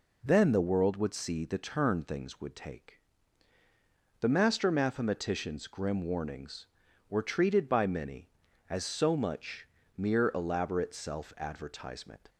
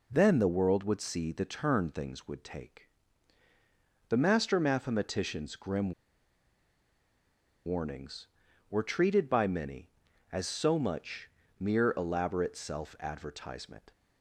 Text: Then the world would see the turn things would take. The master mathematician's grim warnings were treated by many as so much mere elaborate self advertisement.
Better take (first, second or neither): first